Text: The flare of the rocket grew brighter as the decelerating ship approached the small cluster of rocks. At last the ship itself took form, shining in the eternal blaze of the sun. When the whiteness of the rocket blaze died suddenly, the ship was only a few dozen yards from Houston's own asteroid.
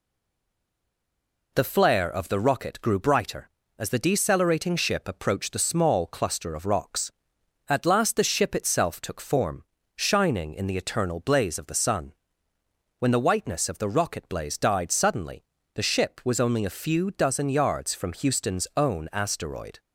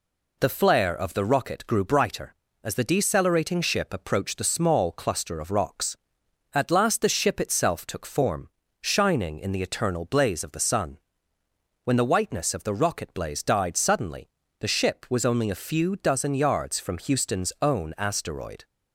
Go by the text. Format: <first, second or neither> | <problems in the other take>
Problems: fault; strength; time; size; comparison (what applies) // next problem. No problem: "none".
second | stays silent before the first word; noticeable; until 1.5 s; 1.5 s long